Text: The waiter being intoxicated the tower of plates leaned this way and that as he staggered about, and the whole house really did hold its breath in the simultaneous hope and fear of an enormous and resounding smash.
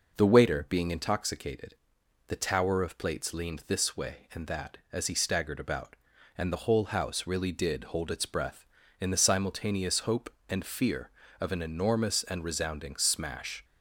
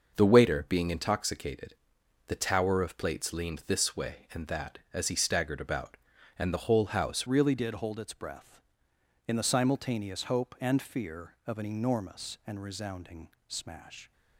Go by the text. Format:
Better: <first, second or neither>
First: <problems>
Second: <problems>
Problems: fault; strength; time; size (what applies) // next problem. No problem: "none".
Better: first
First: pauses between "intoxicated" and "the"; noticeable; at 1.7 s; 0.52 s long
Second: starts louder than the rest; noticeable; until 1.1 s; 6 dB // pauses between "intoxicated" and "the"; noticeable; at 1.7 s; 0.52 s long // changes voice at "really"; from 7.2 s on; 6.9 s long // pauses between "resounding" and "smash"; slight; at 13.2 s; 0.18 s long